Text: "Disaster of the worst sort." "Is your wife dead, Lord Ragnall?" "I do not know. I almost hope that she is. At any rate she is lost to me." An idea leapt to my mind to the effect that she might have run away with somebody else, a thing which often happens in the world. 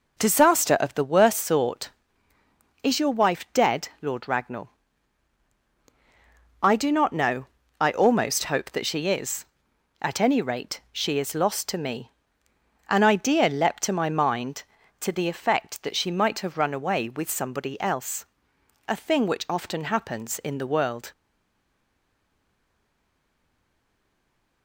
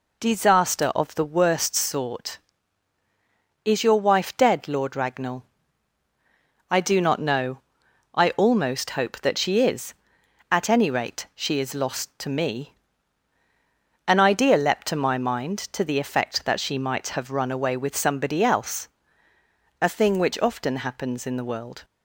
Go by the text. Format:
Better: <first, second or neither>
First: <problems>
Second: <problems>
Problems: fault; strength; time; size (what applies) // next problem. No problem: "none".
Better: second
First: stays silent after the last word; strong; from 21.1 s on; 3.5 s long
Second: none